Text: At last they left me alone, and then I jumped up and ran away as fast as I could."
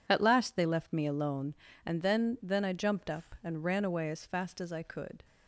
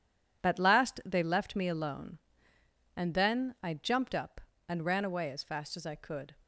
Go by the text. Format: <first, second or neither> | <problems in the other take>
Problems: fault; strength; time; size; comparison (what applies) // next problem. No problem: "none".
second | says "then" twice; at 2.4 s